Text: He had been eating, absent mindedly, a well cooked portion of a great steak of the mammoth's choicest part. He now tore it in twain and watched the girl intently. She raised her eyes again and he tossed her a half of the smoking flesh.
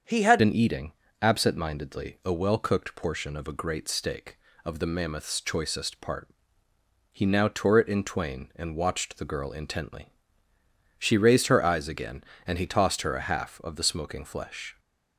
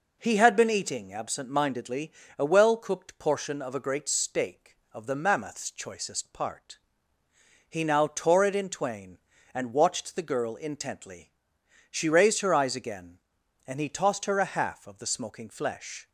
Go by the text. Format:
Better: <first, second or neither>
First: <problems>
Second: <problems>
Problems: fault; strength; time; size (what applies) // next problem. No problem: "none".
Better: second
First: starts louder than the rest; until 1.3 s; 7 dB // changes voice at "been"; from 0.3 s on; 14.4 s long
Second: none